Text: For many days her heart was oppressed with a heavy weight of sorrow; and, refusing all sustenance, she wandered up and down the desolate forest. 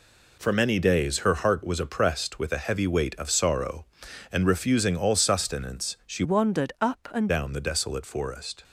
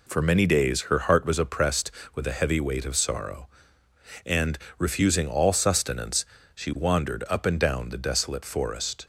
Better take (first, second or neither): second